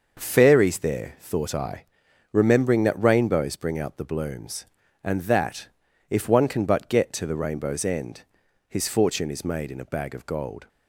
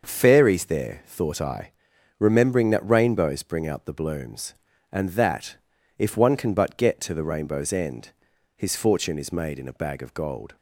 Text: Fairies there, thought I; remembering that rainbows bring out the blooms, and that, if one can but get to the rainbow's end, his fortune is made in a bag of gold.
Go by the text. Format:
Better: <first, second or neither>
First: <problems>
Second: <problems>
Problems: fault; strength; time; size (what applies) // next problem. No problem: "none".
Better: neither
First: starts louder than the rest; noticeable; until 1.2 s; 6 dB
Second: starts louder than the rest; noticeable; until 1.1 s; 6 dB